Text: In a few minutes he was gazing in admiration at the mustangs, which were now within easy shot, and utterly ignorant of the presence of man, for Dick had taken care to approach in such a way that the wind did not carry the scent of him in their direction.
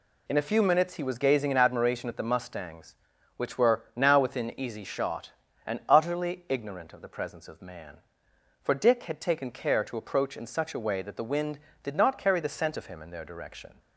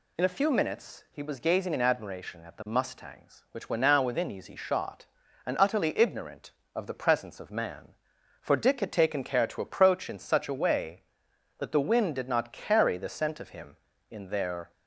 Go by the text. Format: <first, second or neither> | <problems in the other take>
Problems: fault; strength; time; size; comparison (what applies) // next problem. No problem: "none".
first | stops before "direction"; at 14.7 s